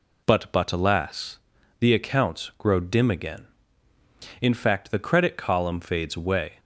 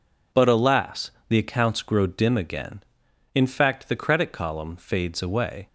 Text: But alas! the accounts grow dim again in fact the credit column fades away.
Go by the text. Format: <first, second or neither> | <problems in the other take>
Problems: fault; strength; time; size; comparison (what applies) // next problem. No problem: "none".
second | says "But" twice; at 0.5 s